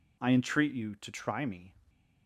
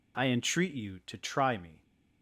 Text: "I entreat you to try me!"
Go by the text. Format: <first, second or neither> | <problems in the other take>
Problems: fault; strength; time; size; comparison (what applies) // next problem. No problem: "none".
neither | none